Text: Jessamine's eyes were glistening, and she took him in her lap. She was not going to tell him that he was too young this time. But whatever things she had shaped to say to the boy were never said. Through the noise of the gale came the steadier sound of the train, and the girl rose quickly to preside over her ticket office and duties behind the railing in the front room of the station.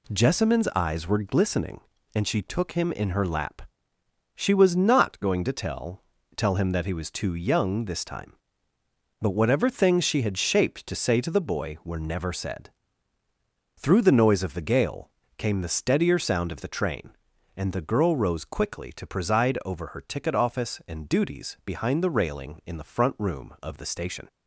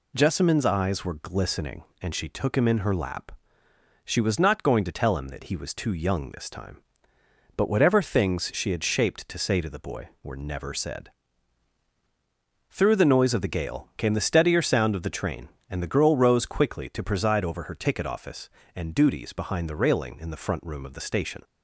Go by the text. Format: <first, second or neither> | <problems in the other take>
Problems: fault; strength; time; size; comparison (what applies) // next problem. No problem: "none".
second | says "tell" twice; at 6.3 s // pauses between "gale" and "came"; slight; at 15.0 s; 0.28 s long